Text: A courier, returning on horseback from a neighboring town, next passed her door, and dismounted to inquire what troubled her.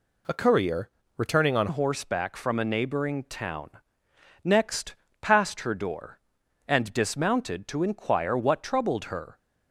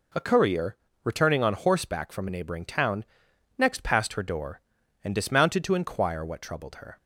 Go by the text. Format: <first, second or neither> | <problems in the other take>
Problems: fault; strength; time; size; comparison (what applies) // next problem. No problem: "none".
second | changes voice at "horseback"; from 1.6 s on; 7.7 s long // pauses between "next" and "passed"; slight; at 4.9 s; 0.26 s long